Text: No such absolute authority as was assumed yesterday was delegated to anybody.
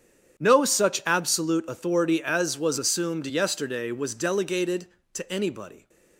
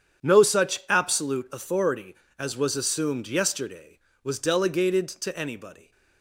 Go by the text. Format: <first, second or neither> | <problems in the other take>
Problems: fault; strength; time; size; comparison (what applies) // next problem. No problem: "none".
neither | starts louder than the rest; strong; the same in both